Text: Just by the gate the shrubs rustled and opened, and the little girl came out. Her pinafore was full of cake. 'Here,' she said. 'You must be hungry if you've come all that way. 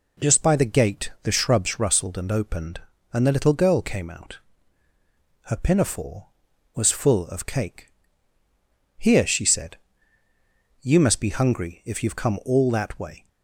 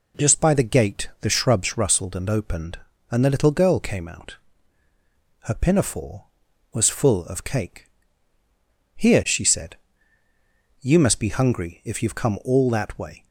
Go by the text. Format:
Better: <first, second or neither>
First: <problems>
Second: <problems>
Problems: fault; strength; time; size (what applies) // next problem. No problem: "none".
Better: neither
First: none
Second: none